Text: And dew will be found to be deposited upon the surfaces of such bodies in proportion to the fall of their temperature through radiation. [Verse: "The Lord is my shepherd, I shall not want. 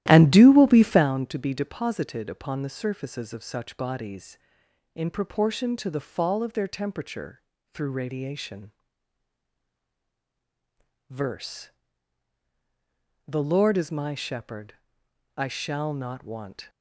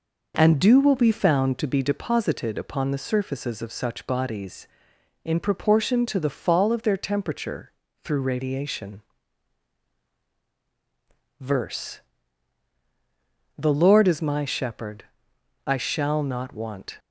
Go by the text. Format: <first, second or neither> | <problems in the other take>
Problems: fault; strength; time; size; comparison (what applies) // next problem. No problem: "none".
second | starts louder than the rest; strong; until 1.1 s; 13.5 dB // pauses between "temperature" and "through"; slight; at 7.4 s; 0.32 s long; slight in the second